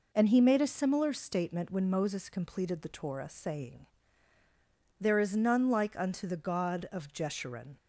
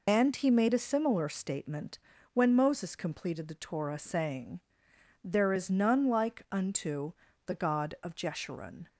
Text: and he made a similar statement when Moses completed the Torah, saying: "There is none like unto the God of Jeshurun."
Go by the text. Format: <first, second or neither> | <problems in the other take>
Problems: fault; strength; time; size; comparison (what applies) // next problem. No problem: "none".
first | loses the start of "and"; at 0.0 s; 70 ms // pauses between "statement" and "when"; slight; at 1.9 s; 0.36 s long // pauses between "unto" and "the"; slight; at 7.1 s; 0.32 s long